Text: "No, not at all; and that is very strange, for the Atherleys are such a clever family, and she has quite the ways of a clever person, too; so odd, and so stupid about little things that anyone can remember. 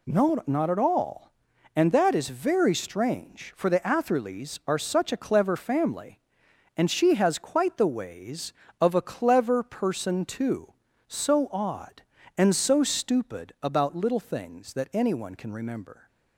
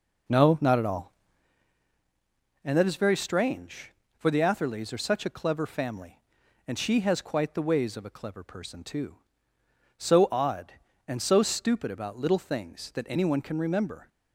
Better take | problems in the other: first | starts louder than the rest; noticeable; until 1.5 s; 4.5 dB

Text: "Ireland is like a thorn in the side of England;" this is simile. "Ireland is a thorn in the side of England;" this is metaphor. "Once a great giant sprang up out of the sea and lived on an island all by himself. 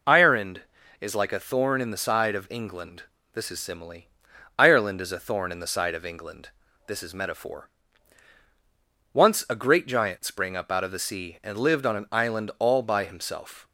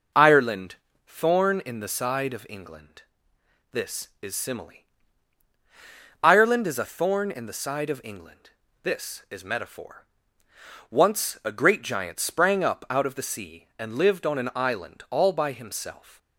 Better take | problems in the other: first | skips "is like a"; at 0.9 s

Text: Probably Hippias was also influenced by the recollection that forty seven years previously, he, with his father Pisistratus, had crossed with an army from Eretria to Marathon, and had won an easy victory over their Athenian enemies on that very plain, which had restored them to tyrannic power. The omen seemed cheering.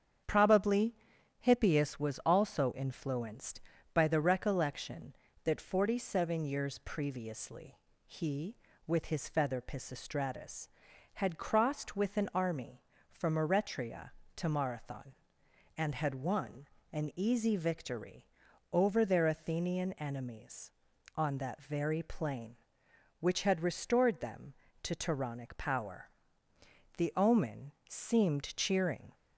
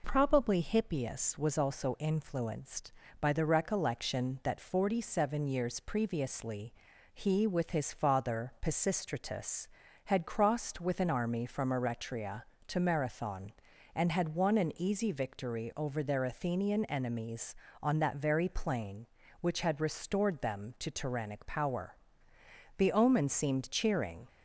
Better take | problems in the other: second | starts louder than the rest; strong; until 1.7 s; 8 dB // pauses between "Probably" and "Hippias"; noticeable; at 0.9 s; 0.46 s long // says "feather" for "father"; at 9.2 s // pauses between "won" and "an"; slight; at 16.6 s; 0.26 s long // pauses between "victory" and "over"; noticeable; at 18.2 s; 0.46 s long // pauses between "omen" and "seemed"; slight; at 27.7 s; 0.16 s long

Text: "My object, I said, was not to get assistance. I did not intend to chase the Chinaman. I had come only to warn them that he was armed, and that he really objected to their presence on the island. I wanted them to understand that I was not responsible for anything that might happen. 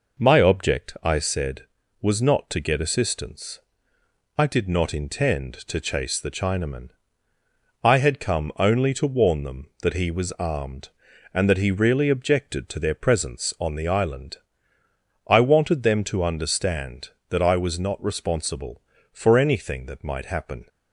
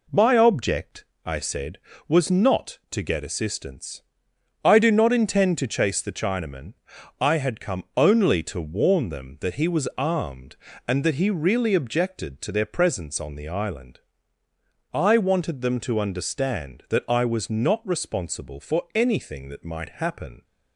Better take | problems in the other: first | says "do" for "did"; at 4.7 s

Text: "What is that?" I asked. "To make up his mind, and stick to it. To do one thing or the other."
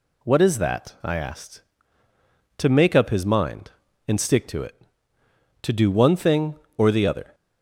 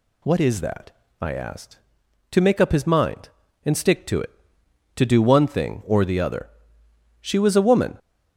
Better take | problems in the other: first | goes on to say "She was a woman"; noticeable; from 7.2 s on; 0.78 s long

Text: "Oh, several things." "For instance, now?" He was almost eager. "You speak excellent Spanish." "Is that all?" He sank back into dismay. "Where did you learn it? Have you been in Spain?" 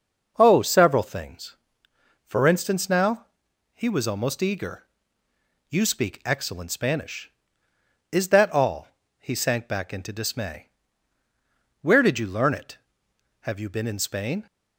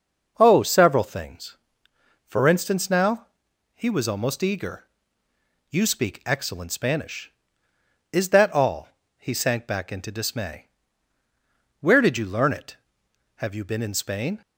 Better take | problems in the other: neither | none

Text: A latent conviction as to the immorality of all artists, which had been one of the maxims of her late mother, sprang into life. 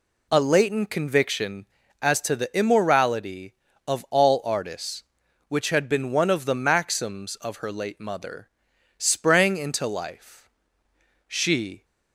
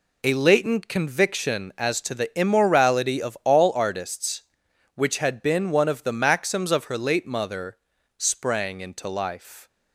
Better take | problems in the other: second | goes on to say "She"; from 11.2 s on; 0.58 s long

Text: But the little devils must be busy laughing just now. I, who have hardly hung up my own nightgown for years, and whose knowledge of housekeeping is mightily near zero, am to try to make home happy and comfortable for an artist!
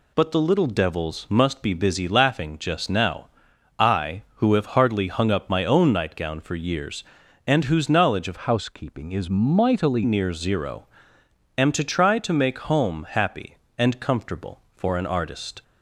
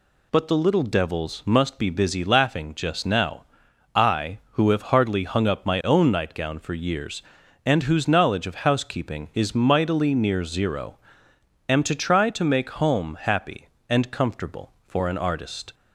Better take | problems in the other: second | changes voice from "housekeeping" to "mightily"; from 8.3 to 10.0 s; 1.7 s long

